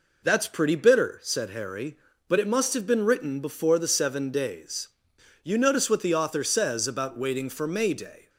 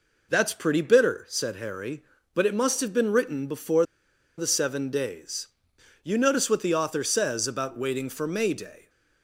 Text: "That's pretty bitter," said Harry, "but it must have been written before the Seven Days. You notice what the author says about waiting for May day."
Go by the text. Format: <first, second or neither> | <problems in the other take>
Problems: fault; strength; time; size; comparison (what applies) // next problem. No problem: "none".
first | pauses between "before" and "the"; noticeable; at 3.8 s; 0.53 s long